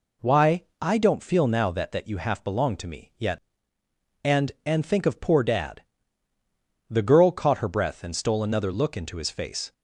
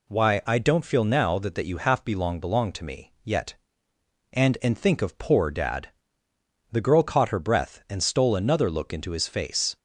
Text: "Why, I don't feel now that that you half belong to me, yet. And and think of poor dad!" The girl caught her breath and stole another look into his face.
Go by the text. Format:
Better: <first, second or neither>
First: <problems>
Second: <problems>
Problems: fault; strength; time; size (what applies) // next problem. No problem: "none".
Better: first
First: none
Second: says "belong" twice; at 2.4 s